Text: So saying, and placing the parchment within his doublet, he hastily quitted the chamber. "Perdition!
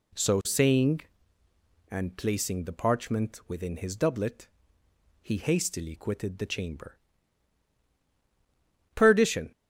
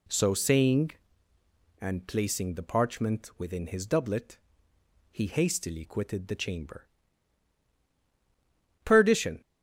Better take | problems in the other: neither | none

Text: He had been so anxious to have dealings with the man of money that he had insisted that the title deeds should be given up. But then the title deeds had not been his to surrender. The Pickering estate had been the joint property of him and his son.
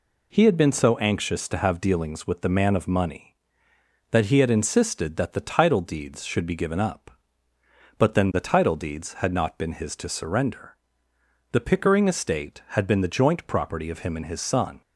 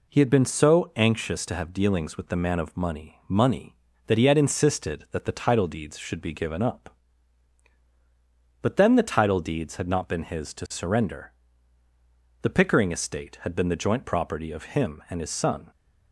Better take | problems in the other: first | says "money" twice; at 3.2 s

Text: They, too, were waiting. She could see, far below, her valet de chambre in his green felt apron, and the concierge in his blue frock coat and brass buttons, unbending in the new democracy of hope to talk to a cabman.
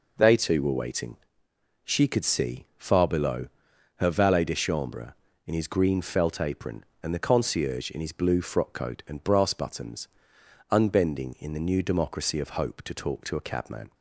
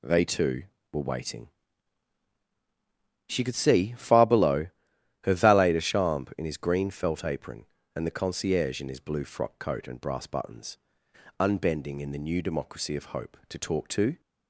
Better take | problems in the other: first | stops before "a cabman"; at 14.2 s

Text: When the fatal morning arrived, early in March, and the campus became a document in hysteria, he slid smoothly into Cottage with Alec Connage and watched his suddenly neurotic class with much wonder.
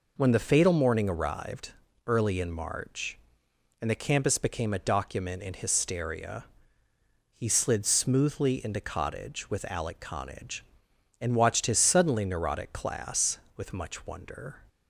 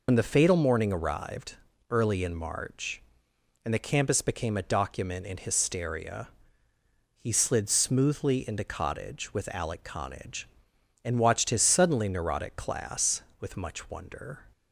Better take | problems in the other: first | loses the start of "When"; at 0.0 s; 65 ms

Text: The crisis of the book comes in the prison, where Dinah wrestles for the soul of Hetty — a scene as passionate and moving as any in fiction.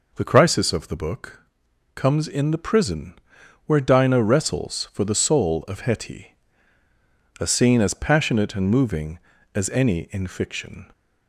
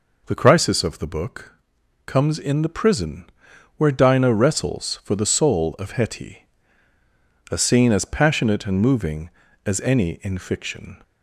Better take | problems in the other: neither | pauses between "book" and "comes"; noticeable; the same in both

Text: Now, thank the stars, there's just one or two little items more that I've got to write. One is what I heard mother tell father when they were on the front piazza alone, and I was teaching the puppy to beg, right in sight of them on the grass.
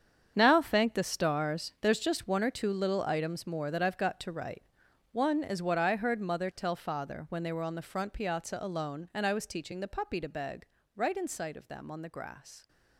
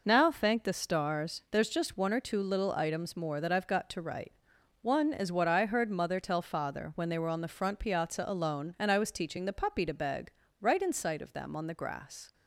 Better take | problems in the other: second | gets quieter; strong; throughout; 13 dB

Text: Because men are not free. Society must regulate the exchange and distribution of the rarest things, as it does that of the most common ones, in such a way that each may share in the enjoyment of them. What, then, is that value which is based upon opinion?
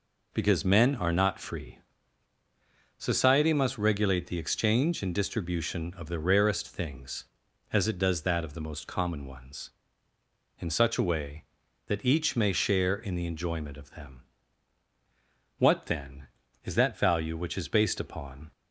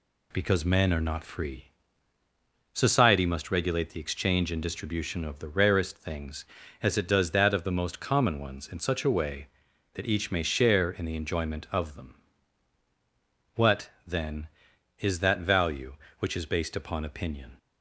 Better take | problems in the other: second | stops before "opinion"; at 18.5 s

